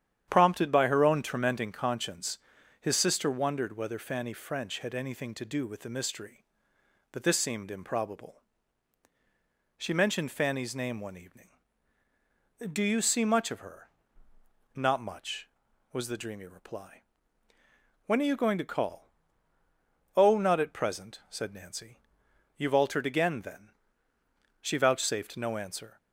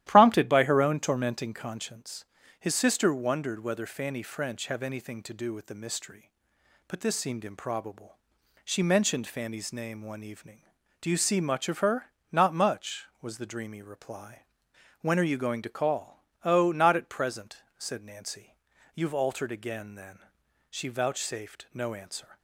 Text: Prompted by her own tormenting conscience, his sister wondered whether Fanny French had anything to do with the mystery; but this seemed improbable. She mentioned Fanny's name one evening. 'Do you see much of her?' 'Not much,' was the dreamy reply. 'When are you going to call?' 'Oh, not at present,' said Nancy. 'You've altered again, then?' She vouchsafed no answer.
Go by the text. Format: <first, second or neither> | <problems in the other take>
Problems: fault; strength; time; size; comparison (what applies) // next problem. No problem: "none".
first | starts louder than the rest; strong; until 1.0 s; 13 dB; strong in the first // says "have" for "had"; at 4.6 s